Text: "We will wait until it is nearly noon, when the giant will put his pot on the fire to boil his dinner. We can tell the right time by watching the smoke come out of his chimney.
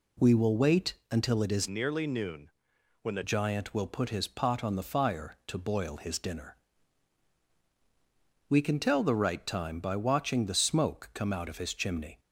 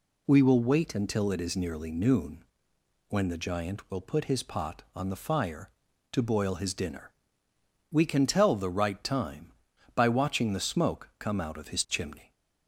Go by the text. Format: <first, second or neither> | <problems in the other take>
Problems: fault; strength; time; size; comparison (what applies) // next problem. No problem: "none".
second | pauses between "wait" and "until"; slight; at 0.9 s; 0.18 s long // changes voice from "nearly" to "the"; from 1.6 to 3.2 s; 1.6 s long